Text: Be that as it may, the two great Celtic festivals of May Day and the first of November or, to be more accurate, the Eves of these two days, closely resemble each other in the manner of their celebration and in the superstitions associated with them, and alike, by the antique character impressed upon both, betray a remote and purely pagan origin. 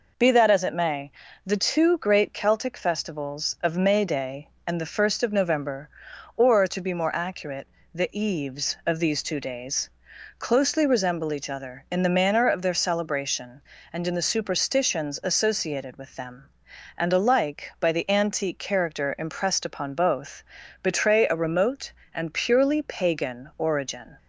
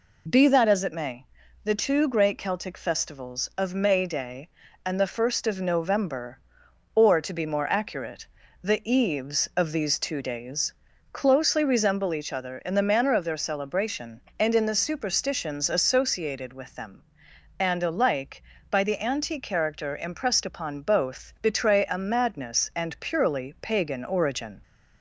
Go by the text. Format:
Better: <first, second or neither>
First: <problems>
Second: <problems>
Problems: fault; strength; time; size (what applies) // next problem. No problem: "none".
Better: first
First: none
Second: says "madness" for "remote"; at 21.9 s